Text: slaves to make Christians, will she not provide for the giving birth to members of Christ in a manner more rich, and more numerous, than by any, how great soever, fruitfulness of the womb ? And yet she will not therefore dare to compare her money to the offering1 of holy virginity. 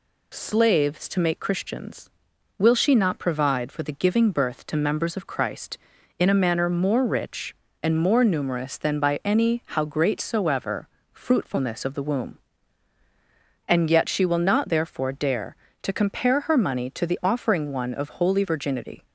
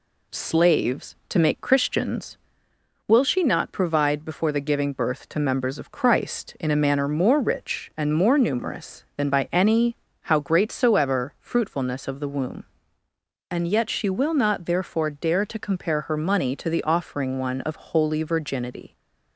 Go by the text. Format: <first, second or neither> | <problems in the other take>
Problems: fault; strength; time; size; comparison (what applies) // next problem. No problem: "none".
first | says "before" for "for"; at 4.2 s